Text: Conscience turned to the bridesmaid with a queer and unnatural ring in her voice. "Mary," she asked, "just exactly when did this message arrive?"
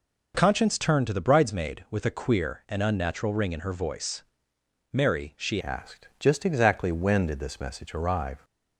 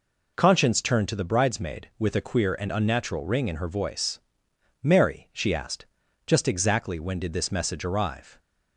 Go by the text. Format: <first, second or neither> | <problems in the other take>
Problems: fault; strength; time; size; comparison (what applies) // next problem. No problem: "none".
second | changes voice at "asked"; from 5.6 s on; 2.8 s long